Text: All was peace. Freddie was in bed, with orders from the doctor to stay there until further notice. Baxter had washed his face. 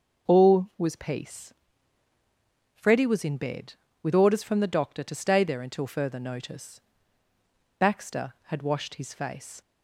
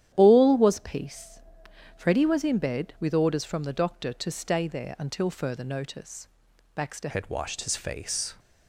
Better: first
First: starts louder than the rest; until 1.3 s; 6.5 dB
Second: starts louder than the rest; strong; until 1.1 s; 11 dB // changes voice at "had"; from 7.0 s on; 1.3 s long

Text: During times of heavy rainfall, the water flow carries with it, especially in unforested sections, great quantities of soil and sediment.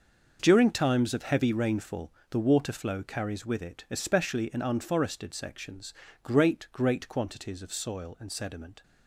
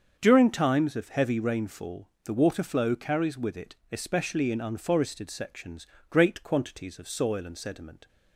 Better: second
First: starts louder than the rest; noticeable; until 1.4 s; 6 dB // says "great" twice; at 6.7 s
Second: starts louder than the rest; until 1.2 s; 7 dB

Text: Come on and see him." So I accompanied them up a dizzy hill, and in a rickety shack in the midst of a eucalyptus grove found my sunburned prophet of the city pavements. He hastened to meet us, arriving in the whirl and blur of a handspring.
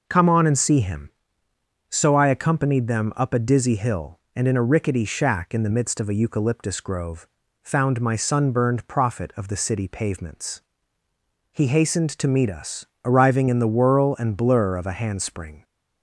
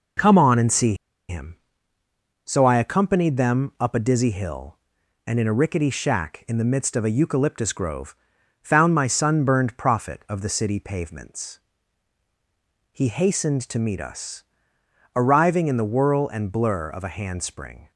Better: first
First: pauses between "grove" and "found"; slight; at 7.2 s; 0.36 s long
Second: pauses between "see" and "him"; slight; at 0.9 s; 0.34 s long // pauses between "grove" and "found"; at 8.1 s; 0.44 s long

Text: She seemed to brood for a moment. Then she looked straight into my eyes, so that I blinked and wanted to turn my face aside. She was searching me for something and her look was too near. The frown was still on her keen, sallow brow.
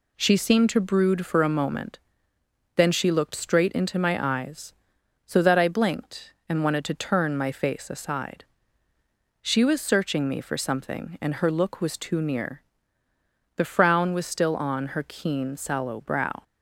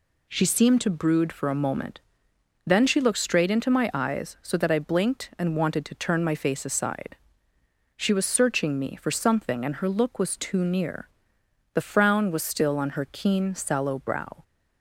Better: neither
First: none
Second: none

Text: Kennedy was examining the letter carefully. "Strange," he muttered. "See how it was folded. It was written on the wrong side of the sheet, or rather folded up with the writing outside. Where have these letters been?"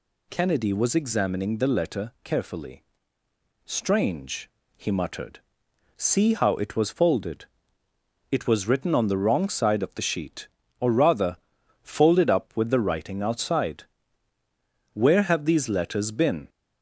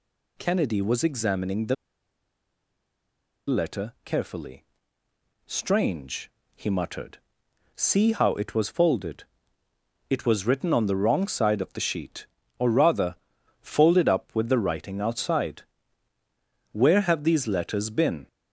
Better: first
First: pauses between "rather" and "folded"; noticeable; at 11.3 s; 0.46 s long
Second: pauses between "the" and "letter"; strong; at 1.7 s; 1.7 s long // pauses between "rather" and "folded"; noticeable; at 13.1 s; 0.46 s long

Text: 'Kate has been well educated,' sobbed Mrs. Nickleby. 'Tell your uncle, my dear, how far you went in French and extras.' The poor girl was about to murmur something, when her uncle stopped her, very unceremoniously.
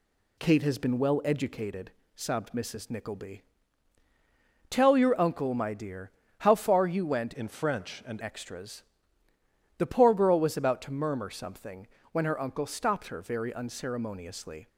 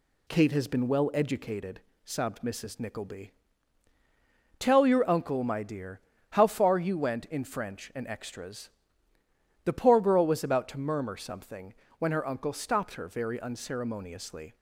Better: second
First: changes voice from "in" to "and"; from 7.3 to 8.2 s; 0.9 s long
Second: none

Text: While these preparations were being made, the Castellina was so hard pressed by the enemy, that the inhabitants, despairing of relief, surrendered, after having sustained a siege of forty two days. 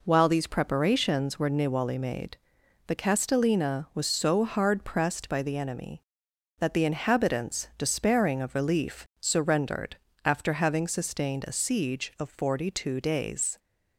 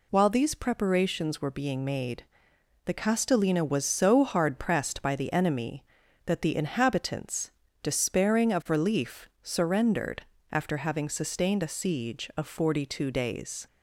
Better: second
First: says "niwali" for "being"; at 1.5 s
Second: none

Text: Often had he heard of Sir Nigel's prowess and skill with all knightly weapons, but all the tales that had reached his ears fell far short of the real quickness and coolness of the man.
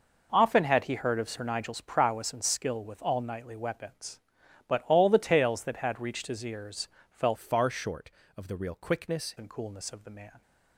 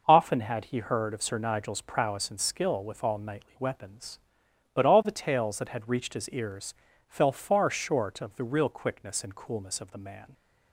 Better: second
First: pauses between "ears" and "fell"; slight; at 6.8 s; 0.24 s long // changes voice from "far" to "quickness"; from 7.3 to 9.3 s; 2.0 s long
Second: pauses between "ears" and "fell"; slight; at 6.7 s; 0.34 s long

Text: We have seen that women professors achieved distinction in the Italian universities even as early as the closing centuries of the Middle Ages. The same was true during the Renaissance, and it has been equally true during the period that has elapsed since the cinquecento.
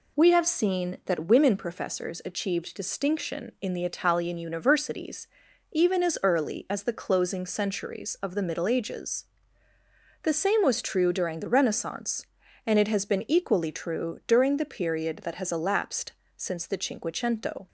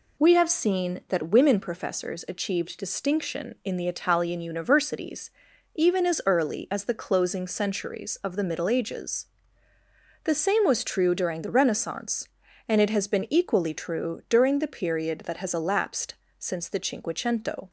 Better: neither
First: pauses between "universities" and "even"; noticeable; at 5.2 s; 0.46 s long // pauses between "elapsed" and "since"; slight; at 16.1 s; 0.26 s long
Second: pauses between "universities" and "even"; noticeable; at 5.2 s; 0.46 s long // pauses between "elapsed" and "since"; slight; at 16.1 s; 0.26 s long

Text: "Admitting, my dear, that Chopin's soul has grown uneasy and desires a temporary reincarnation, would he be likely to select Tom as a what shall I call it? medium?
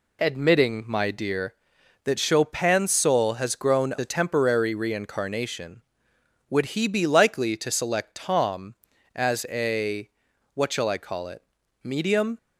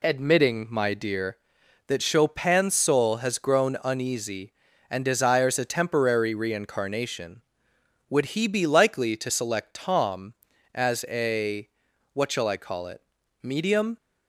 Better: second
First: skips "uneasy and desires"; at 3.9 s // pauses between "a" and "what"; noticeable; at 10.0 s; 0.46 s long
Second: pauses between "a" and "what"; noticeable; at 11.6 s; 0.46 s long

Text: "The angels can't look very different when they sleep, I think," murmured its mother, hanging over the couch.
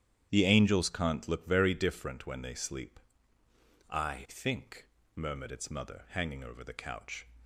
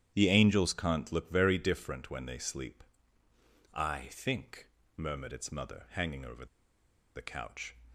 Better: first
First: starts louder than the rest; strong; until 1.3 s; 10 dB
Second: starts louder than the rest; strong; until 1.1 s; 10 dB // pauses between "over" and "the"; noticeable; at 6.4 s; 0.70 s long

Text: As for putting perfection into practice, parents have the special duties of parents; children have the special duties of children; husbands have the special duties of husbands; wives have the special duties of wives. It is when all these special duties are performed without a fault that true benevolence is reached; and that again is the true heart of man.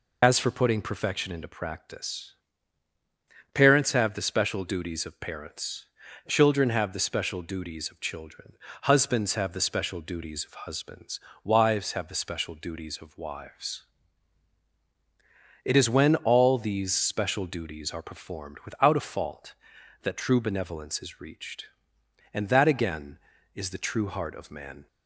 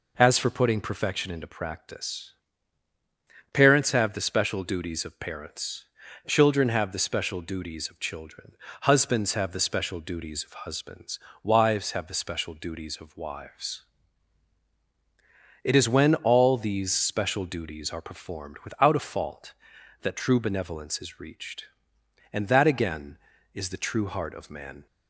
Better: second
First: loses the start of "As"; at 0.2 s; 45 ms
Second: none

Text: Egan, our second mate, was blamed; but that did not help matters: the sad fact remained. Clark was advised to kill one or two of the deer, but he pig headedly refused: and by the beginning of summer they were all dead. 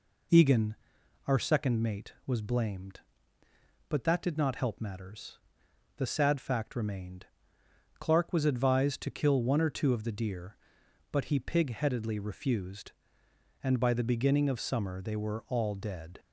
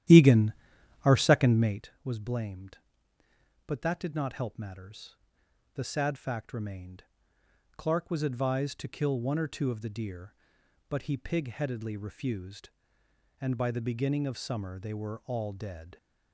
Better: first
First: none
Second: starts louder than the rest; strong; until 1.9 s; 12 dB

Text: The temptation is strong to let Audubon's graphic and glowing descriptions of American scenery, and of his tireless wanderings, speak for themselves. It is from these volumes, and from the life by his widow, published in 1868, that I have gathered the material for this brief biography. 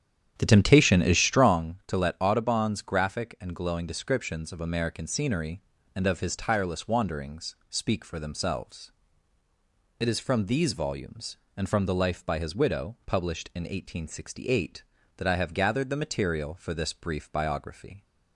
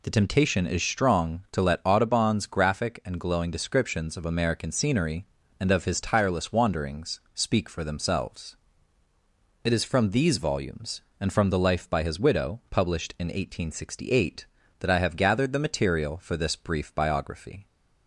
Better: second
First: starts louder than the rest; strong; until 1.7 s; 9 dB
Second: none

